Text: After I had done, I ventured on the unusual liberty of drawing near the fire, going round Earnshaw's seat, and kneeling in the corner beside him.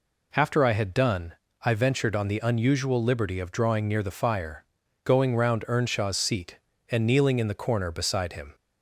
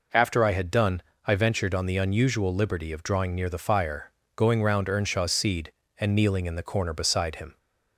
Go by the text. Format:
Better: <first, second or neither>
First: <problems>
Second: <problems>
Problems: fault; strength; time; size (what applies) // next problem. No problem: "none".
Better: first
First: none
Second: says "seed" for "seat"; at 5.3 s